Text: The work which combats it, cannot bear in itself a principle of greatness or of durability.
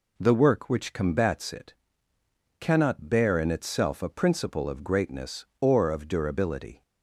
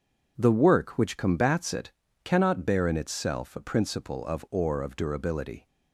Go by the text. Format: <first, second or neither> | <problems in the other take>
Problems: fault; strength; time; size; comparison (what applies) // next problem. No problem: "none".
first | skips "greatness"; at 4.4 s